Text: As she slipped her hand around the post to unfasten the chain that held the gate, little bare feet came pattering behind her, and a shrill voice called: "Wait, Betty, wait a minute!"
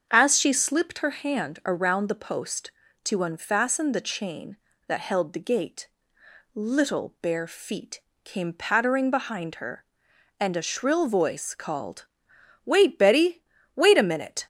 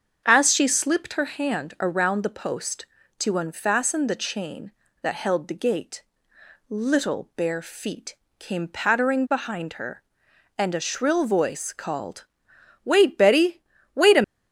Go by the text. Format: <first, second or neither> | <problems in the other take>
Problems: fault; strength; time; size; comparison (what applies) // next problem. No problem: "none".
first | starts louder than the rest; until 1.2 s; 7 dB; also in the first // pauses between "feet" and "came"; slight; at 8.1 s; 0.24 s long; slight in the first // stops before "minute"; at 14.2 s